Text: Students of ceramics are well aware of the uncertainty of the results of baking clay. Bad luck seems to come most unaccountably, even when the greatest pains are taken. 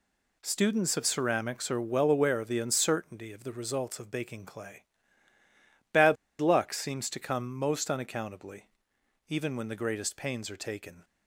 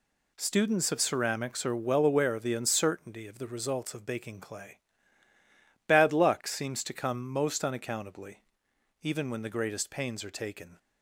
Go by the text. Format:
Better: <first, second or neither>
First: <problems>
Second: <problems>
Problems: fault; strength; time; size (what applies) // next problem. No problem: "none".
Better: second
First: pauses between "Bad" and "luck"; slight; at 6.1 s; 0.24 s long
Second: none